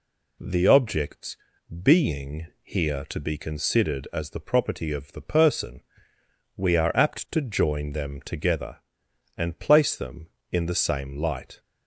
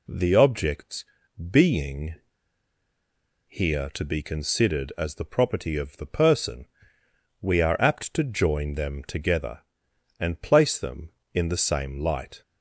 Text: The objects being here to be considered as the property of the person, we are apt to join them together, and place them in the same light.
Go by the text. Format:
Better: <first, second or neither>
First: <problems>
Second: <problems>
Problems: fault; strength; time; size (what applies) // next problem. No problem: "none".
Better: first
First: pauses between "objects" and "being"; noticeable; at 1.3 s; 0.46 s long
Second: pauses between "objects" and "being"; noticeable; at 1.0 s; 0.46 s long // pauses between "being" and "here"; strong; at 2.1 s; 1.3 s long